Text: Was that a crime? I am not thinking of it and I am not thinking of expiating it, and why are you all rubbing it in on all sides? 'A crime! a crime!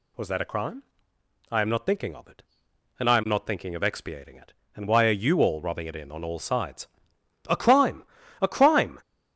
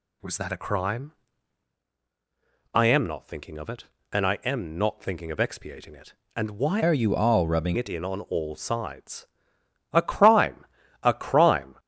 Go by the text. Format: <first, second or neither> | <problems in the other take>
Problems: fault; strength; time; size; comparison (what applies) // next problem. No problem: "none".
first | changes voice from "are" to "rubbing"; from 6.8 to 7.7 s; 0.9 s long